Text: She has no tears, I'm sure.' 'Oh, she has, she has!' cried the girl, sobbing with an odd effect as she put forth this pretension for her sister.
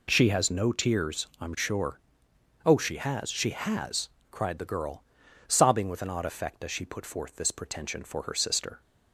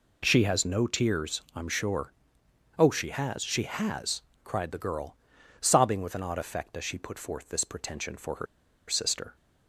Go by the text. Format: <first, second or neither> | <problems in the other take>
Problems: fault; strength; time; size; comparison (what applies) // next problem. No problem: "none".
first | pauses between "her" and "sister"; at 8.4 s; 0.43 s long